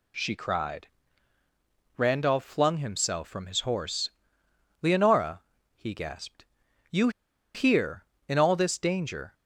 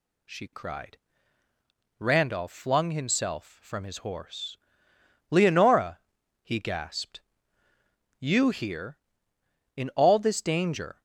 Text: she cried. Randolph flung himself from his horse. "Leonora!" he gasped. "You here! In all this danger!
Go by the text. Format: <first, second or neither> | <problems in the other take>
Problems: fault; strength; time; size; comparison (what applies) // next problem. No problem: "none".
second | pauses between "You" and "here"; at 7.0 s; 0.45 s long